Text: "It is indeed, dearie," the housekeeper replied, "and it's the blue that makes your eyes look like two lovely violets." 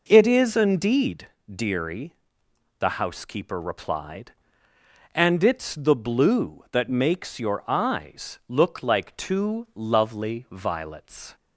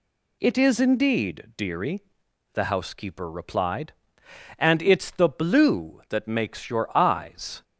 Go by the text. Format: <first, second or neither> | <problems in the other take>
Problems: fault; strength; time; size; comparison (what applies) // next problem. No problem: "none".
first | stops before "look like two lovely violets"; at 7.6 s